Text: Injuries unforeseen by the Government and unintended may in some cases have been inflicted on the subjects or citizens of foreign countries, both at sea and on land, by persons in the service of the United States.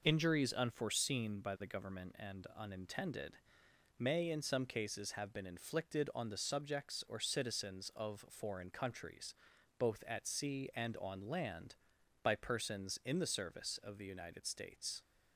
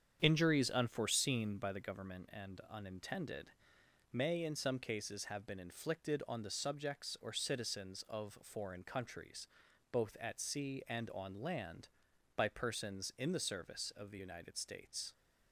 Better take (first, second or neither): first